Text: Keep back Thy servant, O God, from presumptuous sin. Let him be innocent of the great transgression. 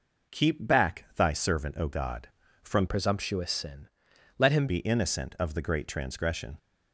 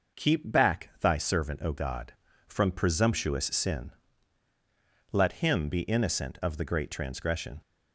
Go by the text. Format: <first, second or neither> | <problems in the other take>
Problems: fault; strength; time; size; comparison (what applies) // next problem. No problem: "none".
second | changes voice from "presumptuous" to "him"; from 2.8 to 4.6 s; 1.8 s long